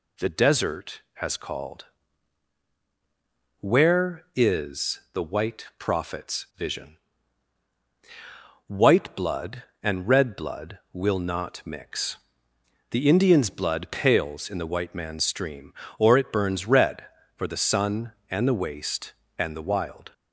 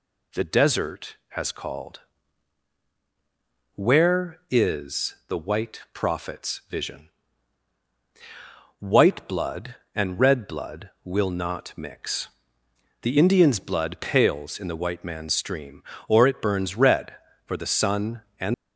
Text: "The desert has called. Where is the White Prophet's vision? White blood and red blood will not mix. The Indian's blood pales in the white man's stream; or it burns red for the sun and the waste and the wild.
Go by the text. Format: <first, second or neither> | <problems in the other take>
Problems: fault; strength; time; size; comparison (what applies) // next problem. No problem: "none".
first | stops before "the waste and the wild"; at 18.5 s